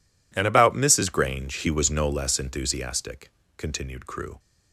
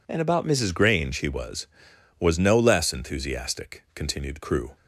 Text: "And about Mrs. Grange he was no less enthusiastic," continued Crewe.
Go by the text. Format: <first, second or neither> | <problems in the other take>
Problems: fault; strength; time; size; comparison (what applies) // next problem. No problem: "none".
first | says "was" twice; at 2.1 s